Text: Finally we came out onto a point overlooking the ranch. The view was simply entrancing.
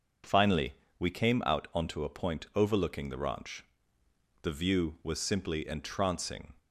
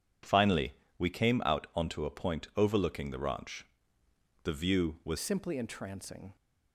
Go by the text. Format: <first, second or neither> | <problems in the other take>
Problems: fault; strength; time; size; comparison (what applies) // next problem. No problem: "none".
first | pauses between "Finally" and "we"; slight; at 0.7 s; 0.26 s long; slight in the first // changes voice at "simply"; from 5.1 s on; 1.2 s long